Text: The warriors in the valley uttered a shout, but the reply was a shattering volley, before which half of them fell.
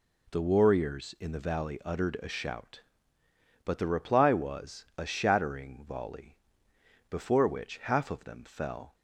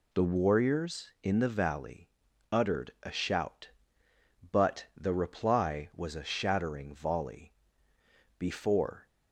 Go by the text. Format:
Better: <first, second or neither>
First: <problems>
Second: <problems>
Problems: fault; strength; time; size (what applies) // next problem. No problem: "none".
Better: first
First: none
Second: pauses between "valley" and "uttered"; at 2.0 s; 0.42 s long // stops before "which half of them fell"; at 9.0 s